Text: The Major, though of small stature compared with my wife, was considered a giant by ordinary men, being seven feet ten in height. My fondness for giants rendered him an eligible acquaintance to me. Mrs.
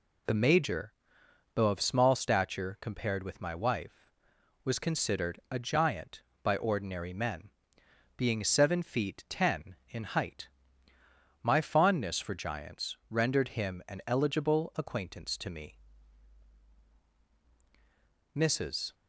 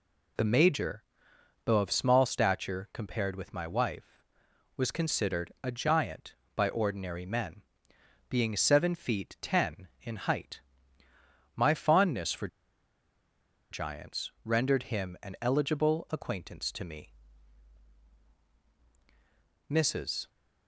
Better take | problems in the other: first | pauses between "for" and "giants"; at 12.4 s; 1.2 s long

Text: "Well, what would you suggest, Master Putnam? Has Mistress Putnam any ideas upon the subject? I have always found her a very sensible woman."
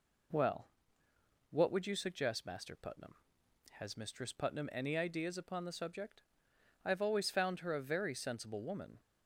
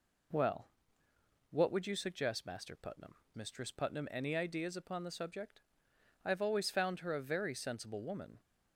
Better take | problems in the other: first | skips "Has"; at 3.2 s

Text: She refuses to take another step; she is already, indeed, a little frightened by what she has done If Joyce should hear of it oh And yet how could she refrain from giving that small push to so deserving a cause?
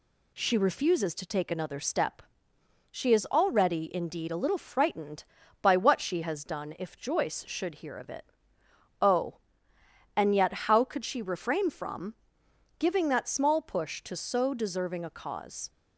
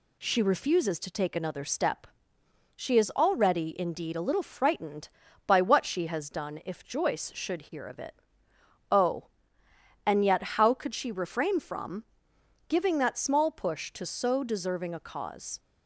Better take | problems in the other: neither | pauses between "it" and "oh"; noticeable; the same in both // pauses between "from" and "giving"; noticeable; the same in both

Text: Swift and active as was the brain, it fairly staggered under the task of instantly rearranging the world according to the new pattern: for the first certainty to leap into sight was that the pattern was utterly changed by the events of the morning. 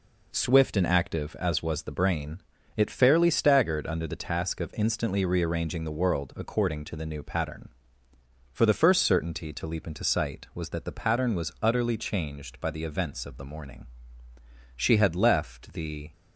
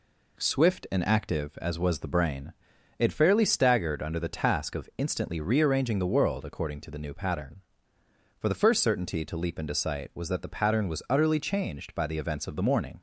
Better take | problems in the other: second | goes on to say "She had left the"; from 14.8 s on; 1.3 s long

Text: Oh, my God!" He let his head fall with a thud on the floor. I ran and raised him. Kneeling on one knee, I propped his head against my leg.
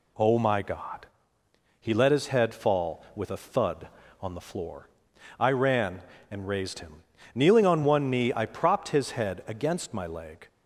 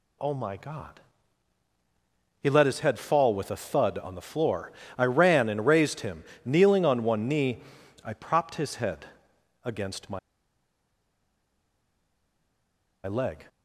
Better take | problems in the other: first | pauses between "head" and "against"; noticeable; at 9.0 s; 0.58 s long // pauses between "my" and "leg"; strong; at 10.1 s; 2.8 s long

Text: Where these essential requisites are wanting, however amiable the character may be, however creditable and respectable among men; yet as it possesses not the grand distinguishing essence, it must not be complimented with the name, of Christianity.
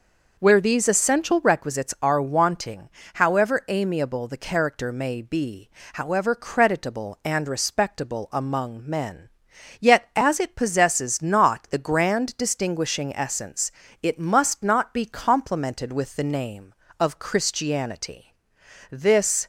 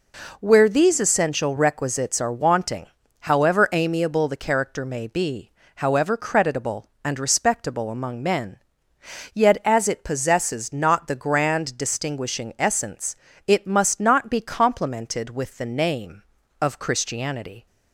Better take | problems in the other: second | goes on to say "This"; from 18.9 s on; 0.56 s long

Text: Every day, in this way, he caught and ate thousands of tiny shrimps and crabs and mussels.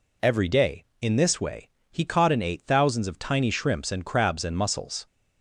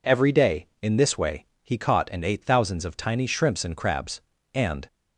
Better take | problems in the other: first | stops before "mussels"; at 4.8 s

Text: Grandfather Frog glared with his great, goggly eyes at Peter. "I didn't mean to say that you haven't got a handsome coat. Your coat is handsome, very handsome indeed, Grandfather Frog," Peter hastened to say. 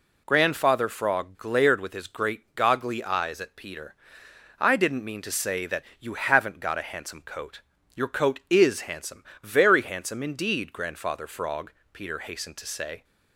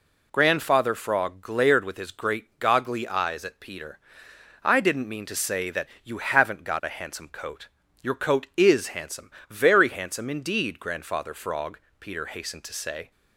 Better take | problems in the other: neither | pauses between "that" and "you"; slight; the same in both

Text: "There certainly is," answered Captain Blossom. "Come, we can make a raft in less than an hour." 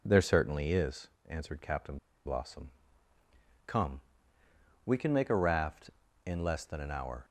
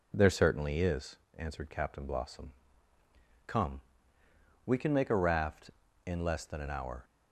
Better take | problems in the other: second | pauses between "Captain" and "Blossom"; slight; at 1.9 s; 0.29 s long

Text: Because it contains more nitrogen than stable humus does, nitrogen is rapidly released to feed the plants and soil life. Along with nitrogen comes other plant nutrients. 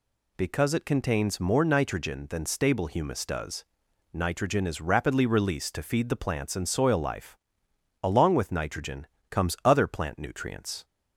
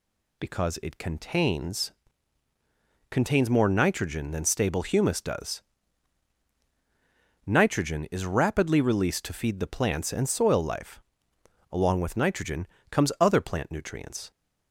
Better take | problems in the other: first | says "contains" twice; at 3.1 s // pauses between "nitrogen" and "comes"; slight; at 12.6 s; 0.24 s long; slight in the first

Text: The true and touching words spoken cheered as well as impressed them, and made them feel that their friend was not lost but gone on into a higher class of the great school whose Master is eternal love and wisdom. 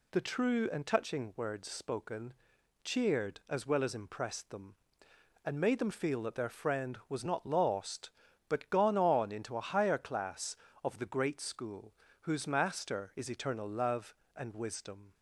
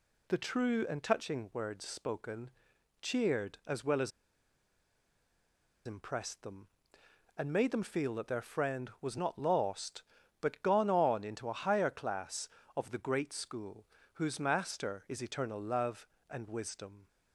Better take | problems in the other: first | pauses between "spoken" and "cheered"; noticeable; at 2.4 s; 0.54 s long; noticeable in the first // pauses between "as" and "impressed"; strong; at 4.1 s; 1.7 s long // pauses between "school" and "whose"; slight; at 13.8 s; 0.28 s long; slight in the first

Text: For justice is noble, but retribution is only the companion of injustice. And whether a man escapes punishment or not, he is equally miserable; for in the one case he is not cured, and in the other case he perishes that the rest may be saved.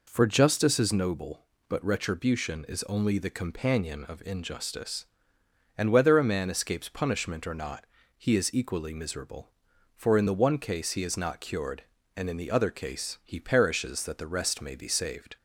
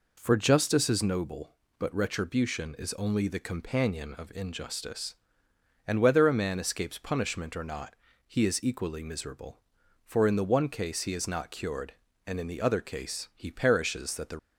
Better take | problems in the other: first | stops before "rest may be saved"; at 14.3 s

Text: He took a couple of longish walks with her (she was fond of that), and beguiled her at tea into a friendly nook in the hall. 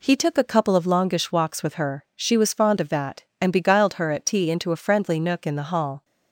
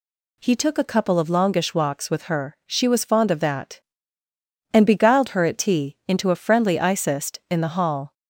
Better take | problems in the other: first | says "icist" for "nook"; at 6.7 s

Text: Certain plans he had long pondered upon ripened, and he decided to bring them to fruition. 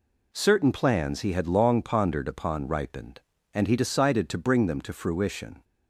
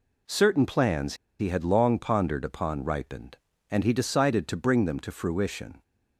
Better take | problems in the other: first | pauses between "plans" and "he"; slight; at 1.1 s; 0.24 s long

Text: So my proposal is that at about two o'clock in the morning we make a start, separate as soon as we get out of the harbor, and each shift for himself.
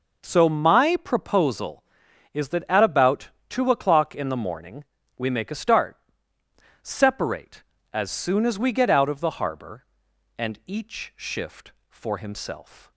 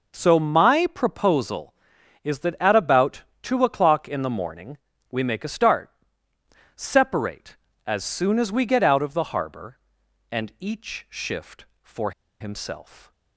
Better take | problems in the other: first | pauses between "about" and "two"; slight; at 3.2 s; 0.20 s long; slight in the first // pauses between "morning" and "we"; slight; at 4.7 s; 0.32 s long; slight in the first // pauses between "for" and "himself"; slight; at 12.1 s; 0.28 s long

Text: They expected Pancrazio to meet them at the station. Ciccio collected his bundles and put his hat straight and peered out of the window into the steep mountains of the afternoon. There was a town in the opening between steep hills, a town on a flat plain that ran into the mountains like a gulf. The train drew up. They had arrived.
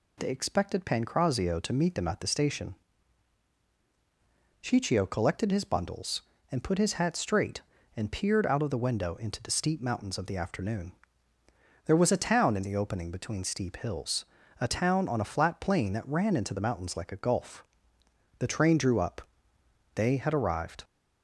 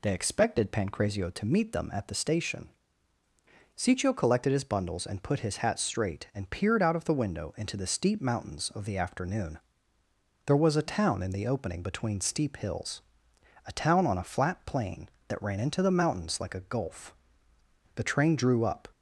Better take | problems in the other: first | stops before "They had arrived"; at 18.9 s

